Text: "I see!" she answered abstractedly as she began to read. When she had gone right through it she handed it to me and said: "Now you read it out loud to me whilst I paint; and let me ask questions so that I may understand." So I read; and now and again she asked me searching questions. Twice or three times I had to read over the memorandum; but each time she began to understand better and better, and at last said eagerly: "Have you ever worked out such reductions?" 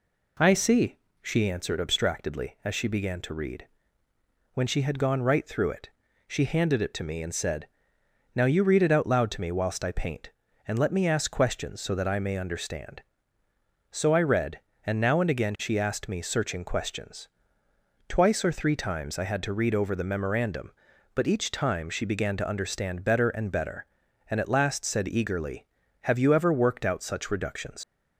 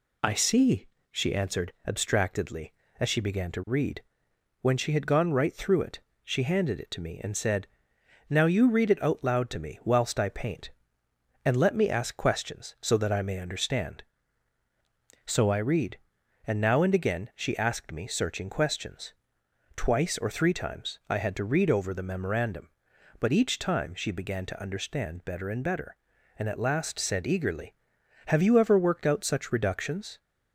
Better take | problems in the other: second | pauses between "it" and "she"; at 5.8 s; 0.38 s long; slight in the second // leaves "reductions" unfinished; at 27.8 s; 100 ms

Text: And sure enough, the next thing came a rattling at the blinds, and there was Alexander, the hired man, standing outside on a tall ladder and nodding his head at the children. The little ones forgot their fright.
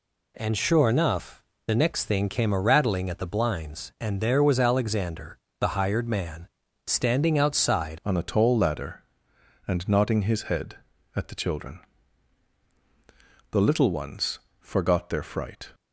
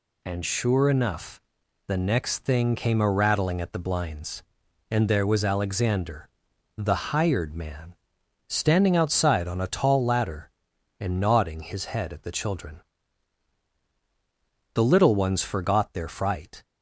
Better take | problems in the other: second | changes voice at "on"; from 8.0 s on; 7.7 s long // pauses between "ones" and "forgot"; slight; at 14.3 s; 0.20 s long

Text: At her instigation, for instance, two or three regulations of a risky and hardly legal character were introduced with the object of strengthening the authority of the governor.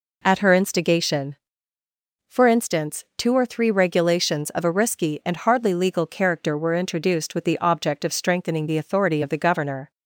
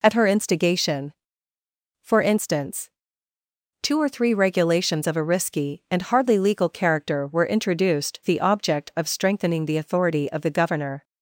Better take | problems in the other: first | skips "with"; at 8.2 s

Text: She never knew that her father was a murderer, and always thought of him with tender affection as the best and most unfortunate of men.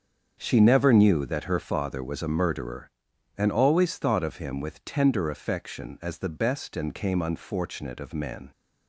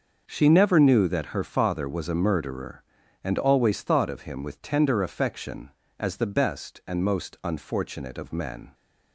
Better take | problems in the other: second | starts louder than the rest; strong; until 1.4 s; 7 dB; also in the second // says "came" for "most"; at 6.9 s

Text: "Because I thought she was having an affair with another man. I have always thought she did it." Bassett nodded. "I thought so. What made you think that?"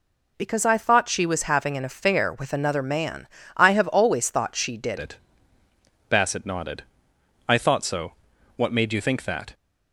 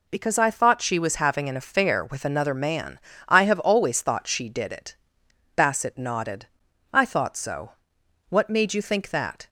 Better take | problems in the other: second | changes voice at "it"; from 4.9 s on; 4.6 s long

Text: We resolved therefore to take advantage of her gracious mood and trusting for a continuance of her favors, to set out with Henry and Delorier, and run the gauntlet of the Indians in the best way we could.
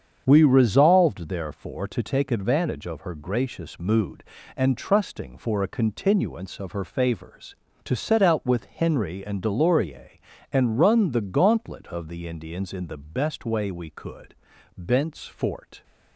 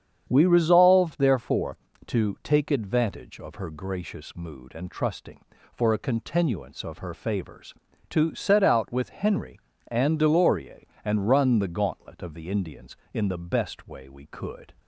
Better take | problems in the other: second | starts louder than the rest; strong; until 1.2 s; 7.5 dB; strong in the second // goes on to say "Bent's Fort"; noticeable; from 14.7 s on; 1.0 s long

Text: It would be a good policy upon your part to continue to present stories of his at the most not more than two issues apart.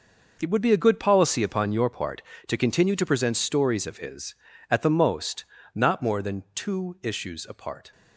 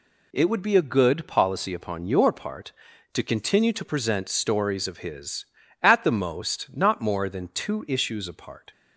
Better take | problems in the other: second | gets quieter; strong; throughout; 11 dB // pauses between "most" and "not"; slight; at 5.4 s; 0.28 s long

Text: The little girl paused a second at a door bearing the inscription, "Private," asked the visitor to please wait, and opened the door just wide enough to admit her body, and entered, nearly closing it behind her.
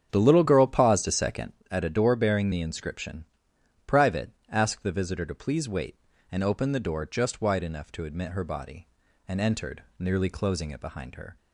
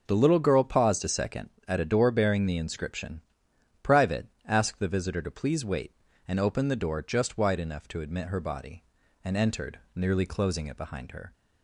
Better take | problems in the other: second | starts louder than the rest; strong; until 1.7 s; 8 dB

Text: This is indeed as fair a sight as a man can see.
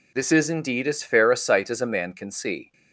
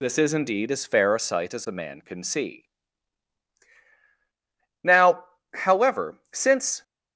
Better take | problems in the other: first | goes on to say "Now however since"; strong; from 4.8 s on; 2.0 s long

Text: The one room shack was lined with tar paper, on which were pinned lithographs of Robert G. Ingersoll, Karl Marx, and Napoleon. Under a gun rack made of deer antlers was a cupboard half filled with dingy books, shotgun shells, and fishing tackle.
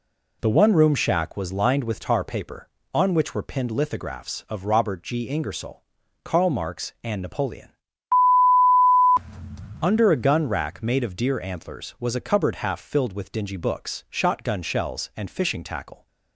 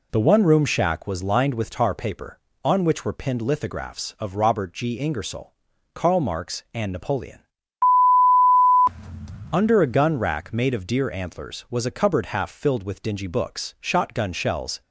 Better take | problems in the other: first | stops before "and fishing tackle"; at 14.8 s

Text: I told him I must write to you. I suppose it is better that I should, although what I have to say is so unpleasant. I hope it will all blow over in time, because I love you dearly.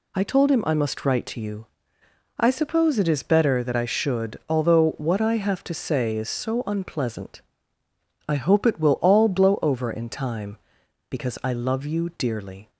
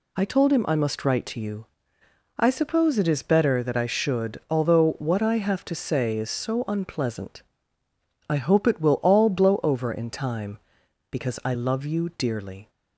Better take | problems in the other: neither | none

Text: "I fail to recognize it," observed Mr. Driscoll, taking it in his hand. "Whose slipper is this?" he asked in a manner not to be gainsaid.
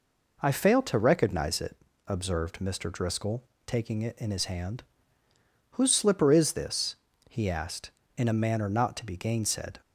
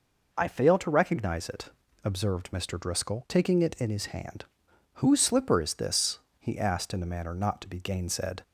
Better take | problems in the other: neither | none

